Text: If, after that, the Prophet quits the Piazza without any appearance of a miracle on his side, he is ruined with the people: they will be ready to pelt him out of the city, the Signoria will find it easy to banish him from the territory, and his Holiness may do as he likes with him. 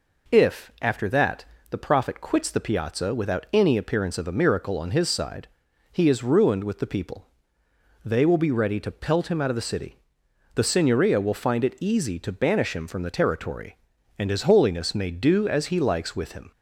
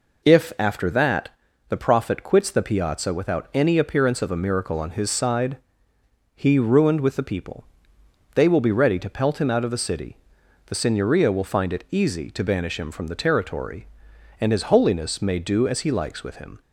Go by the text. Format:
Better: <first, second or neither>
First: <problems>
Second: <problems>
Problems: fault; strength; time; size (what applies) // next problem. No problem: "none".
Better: first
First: none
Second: skips "is"; at 6.5 s